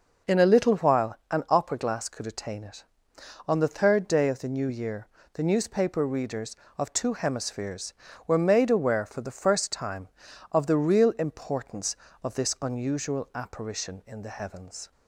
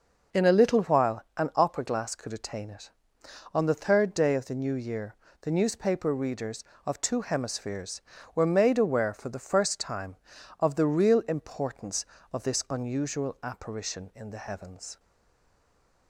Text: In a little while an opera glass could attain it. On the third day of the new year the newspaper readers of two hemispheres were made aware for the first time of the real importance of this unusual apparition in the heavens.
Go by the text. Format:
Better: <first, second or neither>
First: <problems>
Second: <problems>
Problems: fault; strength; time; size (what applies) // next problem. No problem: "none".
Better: first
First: pauses between "year" and "the"; slight; at 5.0 s; 0.24 s long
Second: pauses between "year" and "the"; slight; at 5.1 s; 0.24 s long // stays silent after the last word; from 14.9 s on; 1.1 s long